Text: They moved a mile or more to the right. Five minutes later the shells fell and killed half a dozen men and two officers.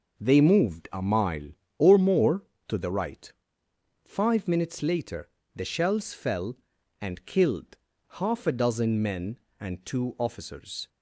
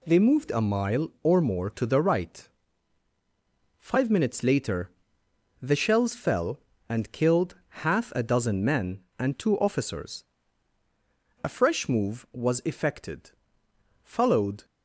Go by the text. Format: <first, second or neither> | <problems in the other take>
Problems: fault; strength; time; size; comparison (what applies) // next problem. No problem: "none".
first | pauses between "later" and "the"; noticeable; at 4.8 s; 0.72 s long; slight in the first // pauses between "killed" and "half"; slight; at 7.5 s; 0.28 s long; slight in the first // goes on to say "A fresh move was effected followed"; strong; from 11.4 s on; 3.2 s long